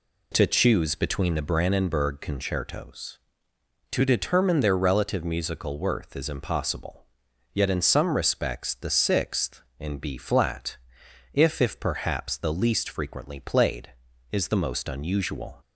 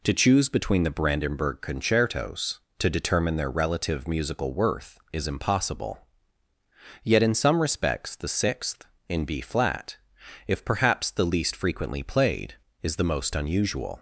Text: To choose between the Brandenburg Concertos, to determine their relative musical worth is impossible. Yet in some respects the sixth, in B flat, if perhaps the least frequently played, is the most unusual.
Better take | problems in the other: second | says "if" twice; at 11.6 s

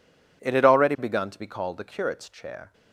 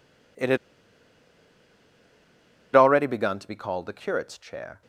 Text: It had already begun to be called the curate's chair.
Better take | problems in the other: first | pauses between "had" and "already"; strong; at 0.5 s; 2.1 s long

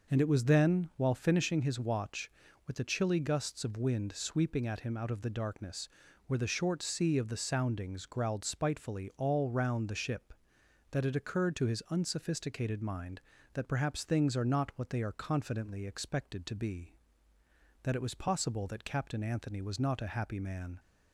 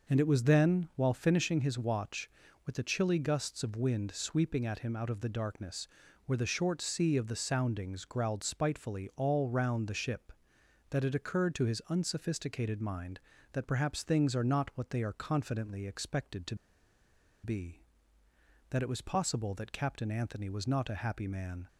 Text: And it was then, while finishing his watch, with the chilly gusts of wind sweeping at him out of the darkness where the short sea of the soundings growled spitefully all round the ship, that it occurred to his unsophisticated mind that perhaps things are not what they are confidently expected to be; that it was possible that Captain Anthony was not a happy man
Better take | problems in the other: first | pauses between "darkness" and "where"; at 5.8 s; 0.38 s long; also in the first // pauses between "to" and "be"; noticeable; at 16.5 s; 0.88 s long

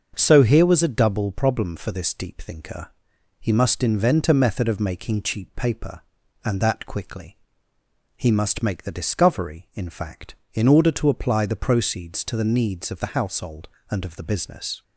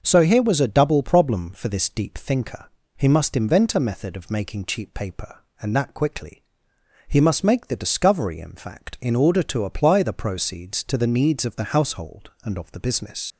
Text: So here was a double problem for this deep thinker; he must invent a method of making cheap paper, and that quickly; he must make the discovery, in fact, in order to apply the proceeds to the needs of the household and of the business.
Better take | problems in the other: first | starts louder than the rest; until 1.0 s; 6.5 dB; also in the first // leaves "business" unfinished; at 13.3 s; 120 ms

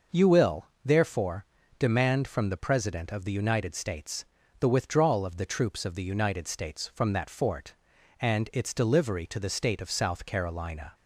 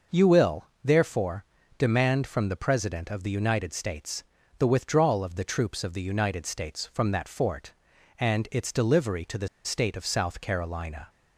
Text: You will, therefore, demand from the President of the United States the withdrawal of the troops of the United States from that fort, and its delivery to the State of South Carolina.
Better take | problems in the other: first | pauses between "States" and "the"; slight; at 4.2 s; 0.36 s long; slight in the first // pauses between "the" and "State"; slight; at 9.4 s; 0.16 s long

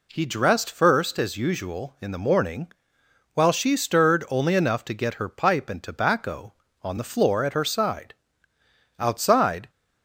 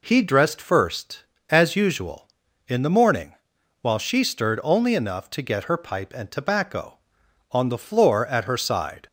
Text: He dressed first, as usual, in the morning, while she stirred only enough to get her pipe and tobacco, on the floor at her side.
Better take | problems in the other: second | goes on to say "Outside"; noticeable; from 8.9 s on; 0.72 s long

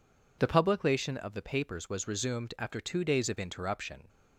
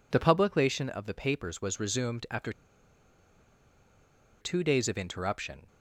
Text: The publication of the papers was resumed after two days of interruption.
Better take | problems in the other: first | pauses between "after" and "two"; strong; at 2.5 s; 1.9 s long

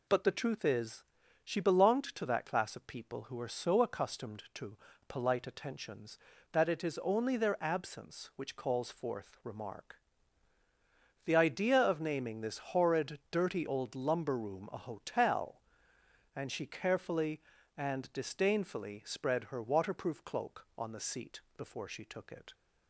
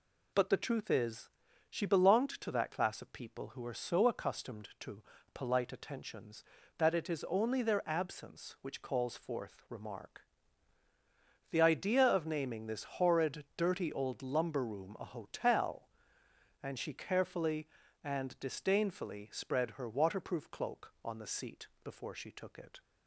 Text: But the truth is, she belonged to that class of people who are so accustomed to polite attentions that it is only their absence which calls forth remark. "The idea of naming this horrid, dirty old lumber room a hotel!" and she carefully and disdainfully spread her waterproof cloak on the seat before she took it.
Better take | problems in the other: neither | pauses between "to" and "polite"; slight; the same in both // pauses between "seat" and "before"; slight; the same in both

